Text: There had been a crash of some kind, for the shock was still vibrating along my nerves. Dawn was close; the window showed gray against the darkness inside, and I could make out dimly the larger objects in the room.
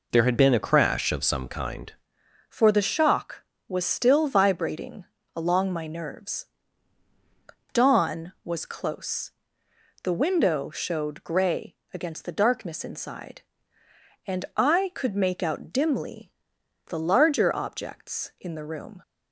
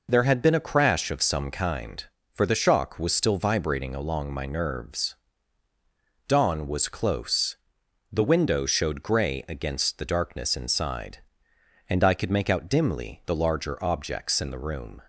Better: second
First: changes voice at "for"; from 2.4 s on; 16.6 s long // pauses between "vibrating" and "along"; slight; at 5.0 s; 0.30 s long // pauses between "gray" and "against"; slight; at 11.7 s; 0.18 s long // pauses between "dimly" and "the"; noticeable; at 16.2 s; 0.56 s long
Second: none

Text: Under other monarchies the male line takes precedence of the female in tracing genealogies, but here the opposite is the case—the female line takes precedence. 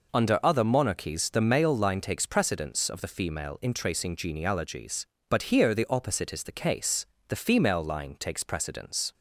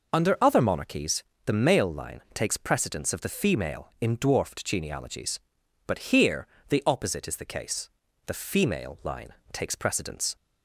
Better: first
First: none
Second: pauses between "monarchies" and "the"; slight; at 1.2 s; 0.22 s long // says "dwarfed" for "tracing"; at 4.1 s // pauses between "here" and "the"; slight; at 6.4 s; 0.22 s long // pauses between "line" and "takes"; slight; at 9.2 s; 0.22 s long

